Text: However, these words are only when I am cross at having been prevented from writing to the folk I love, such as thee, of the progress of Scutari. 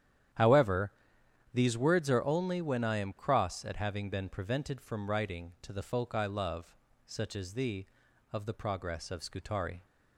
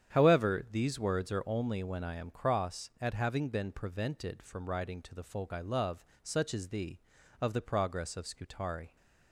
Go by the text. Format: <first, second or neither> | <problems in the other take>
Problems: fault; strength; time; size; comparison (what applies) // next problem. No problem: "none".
neither | starts louder than the rest; strong; the same in both